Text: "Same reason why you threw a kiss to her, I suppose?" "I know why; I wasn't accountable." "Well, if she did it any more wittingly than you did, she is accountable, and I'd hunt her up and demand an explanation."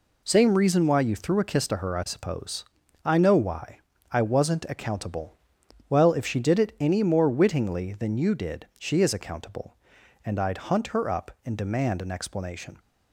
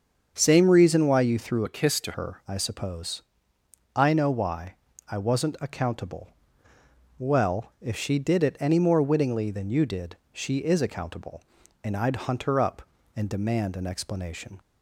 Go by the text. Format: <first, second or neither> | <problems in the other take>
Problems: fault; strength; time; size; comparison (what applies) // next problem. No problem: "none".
first | starts louder than the rest; until 1.3 s; 7 dB // changes voice from "a" to "to"; from 1.6 to 2.1 s; 0.5 s long